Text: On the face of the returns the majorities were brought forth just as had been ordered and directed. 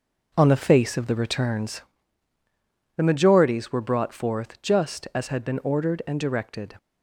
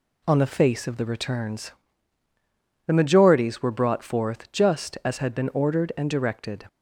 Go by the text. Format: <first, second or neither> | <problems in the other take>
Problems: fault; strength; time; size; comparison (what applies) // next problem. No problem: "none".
second | starts louder than the rest; noticeable; until 2.0 s; 5.5 dB // pauses between "returns" and "the"; at 1.8 s; 1.1 s long; also in the second